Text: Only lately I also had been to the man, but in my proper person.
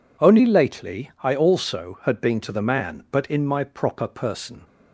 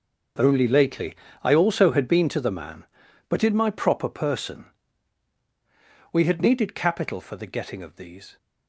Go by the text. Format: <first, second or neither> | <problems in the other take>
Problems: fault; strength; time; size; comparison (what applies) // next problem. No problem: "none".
first | starts louder than the rest; until 1.6 s; 6 dB // pauses between "lately" and "I"; slight; at 1.1 s; 0.28 s long // goes on to say "We had needed capital for the getting of these"; strong; from 6.1 s on; 2.2 s long